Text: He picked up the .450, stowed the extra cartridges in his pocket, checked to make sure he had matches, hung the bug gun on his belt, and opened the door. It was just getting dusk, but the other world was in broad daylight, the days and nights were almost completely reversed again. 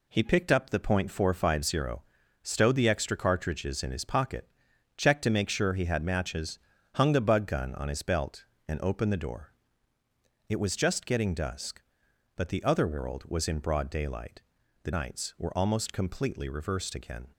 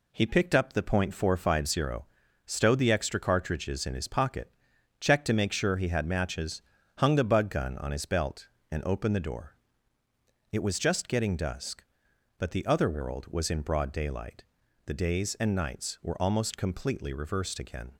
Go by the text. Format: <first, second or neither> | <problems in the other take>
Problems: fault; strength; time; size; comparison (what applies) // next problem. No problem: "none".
second | skips "days and"; at 14.9 s